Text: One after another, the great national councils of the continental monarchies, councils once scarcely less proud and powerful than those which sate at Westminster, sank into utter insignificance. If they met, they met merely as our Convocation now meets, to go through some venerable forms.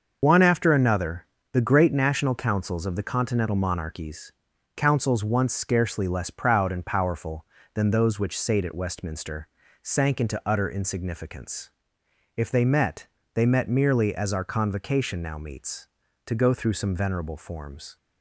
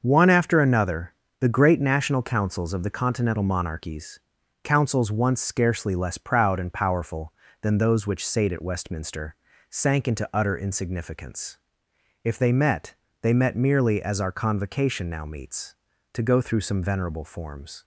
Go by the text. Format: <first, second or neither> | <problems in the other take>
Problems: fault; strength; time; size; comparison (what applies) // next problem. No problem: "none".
second | loses the start of "One"; at 0.2 s; 75 ms // starts louder than the rest; until 1.2 s; 6.5 dB; also in the second